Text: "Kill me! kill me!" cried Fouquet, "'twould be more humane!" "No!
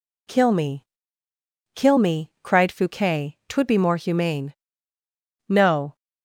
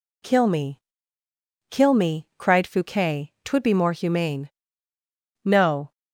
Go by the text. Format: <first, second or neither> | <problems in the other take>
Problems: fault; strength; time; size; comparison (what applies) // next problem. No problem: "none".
neither | none